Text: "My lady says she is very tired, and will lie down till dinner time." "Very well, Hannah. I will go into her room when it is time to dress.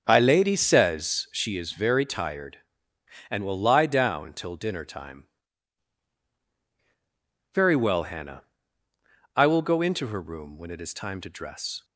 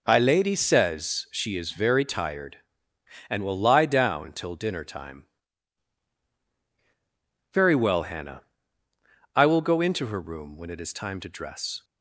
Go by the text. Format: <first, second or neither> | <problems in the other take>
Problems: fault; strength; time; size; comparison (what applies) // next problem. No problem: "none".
second | starts louder than the rest; until 1.6 s; 7 dB